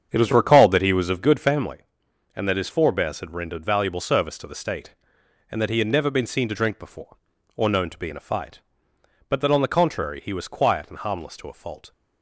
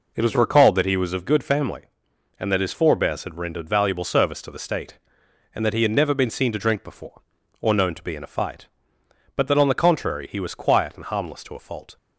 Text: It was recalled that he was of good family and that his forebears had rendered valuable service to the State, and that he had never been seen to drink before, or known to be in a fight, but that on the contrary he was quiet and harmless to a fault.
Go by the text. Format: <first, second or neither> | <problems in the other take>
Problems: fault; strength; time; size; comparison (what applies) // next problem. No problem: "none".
second | starts louder than the rest; strong; until 1.6 s; 7.5 dB